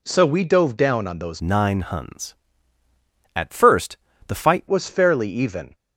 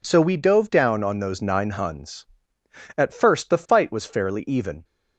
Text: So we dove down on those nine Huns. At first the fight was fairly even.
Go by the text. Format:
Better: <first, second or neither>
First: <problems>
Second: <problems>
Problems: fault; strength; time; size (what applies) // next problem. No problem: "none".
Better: second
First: changes voice from "nine" to "fight"; from 1.4 to 4.6 s; 3.2 s long // pauses between "first" and "the"; slight; at 3.9 s; 0.32 s long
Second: none